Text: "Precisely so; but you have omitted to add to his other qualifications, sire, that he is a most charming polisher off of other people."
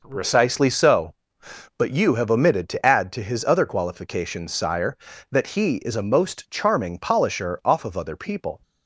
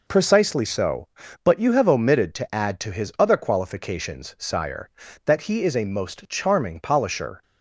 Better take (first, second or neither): first